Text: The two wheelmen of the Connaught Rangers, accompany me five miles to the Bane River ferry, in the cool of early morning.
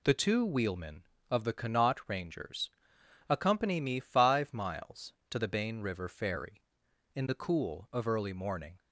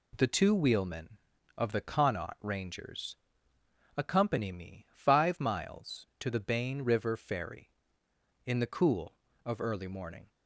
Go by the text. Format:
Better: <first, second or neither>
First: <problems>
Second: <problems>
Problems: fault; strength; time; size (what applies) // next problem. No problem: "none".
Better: neither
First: none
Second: none